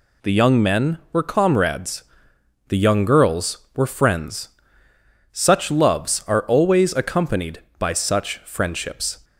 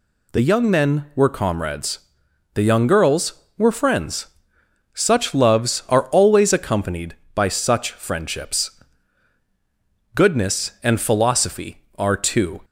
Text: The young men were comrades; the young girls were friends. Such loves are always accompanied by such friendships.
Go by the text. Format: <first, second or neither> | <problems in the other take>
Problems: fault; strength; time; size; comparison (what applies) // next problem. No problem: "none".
first | goes on to say "Goodness and philosophy are two"; strong; from 10.1 s on; 2.4 s long